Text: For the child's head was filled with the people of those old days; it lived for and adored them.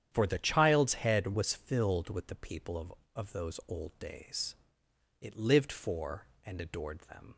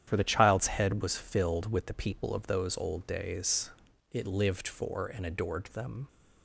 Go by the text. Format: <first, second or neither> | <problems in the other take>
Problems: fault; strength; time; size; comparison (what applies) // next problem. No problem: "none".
second | starts louder than the rest; strong; until 1.1 s; 9 dB; strong in the second // says "of" twice; at 3.1 s